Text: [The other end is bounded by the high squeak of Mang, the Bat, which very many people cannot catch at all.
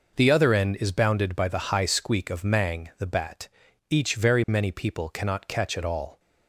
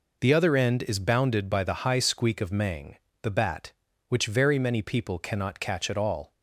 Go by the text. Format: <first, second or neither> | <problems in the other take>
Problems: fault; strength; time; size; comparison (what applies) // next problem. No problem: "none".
second | says "each" for "which"; at 3.8 s